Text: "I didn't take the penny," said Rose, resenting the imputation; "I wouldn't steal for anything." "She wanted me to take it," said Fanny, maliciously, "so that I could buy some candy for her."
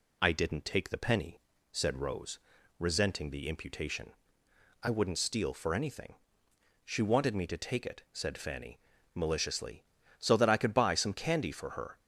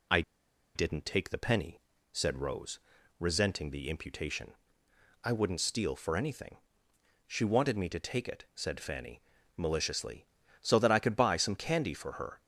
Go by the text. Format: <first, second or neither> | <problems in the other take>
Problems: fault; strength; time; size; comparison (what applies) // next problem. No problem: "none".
first | pauses between "I" and "didn't"; noticeable; at 0.2 s; 0.53 s long